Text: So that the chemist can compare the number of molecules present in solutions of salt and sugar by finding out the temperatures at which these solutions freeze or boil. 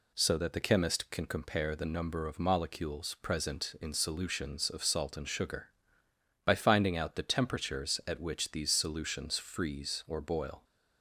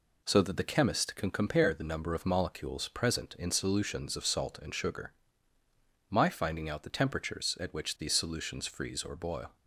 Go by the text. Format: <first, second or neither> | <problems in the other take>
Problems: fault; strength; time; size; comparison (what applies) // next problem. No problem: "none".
first | says "my" for "by"; at 6.0 s